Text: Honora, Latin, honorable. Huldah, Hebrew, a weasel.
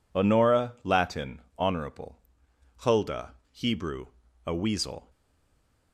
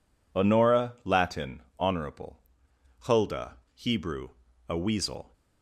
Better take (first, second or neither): second